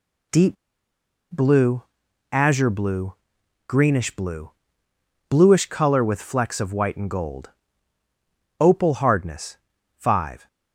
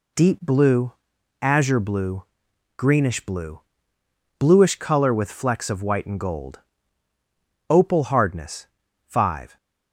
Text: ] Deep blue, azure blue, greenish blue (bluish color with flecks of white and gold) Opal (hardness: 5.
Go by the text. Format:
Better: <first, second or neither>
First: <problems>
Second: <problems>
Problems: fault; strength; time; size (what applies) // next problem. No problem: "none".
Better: second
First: pauses between "Deep" and "blue"; noticeable; at 0.5 s; 0.77 s long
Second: none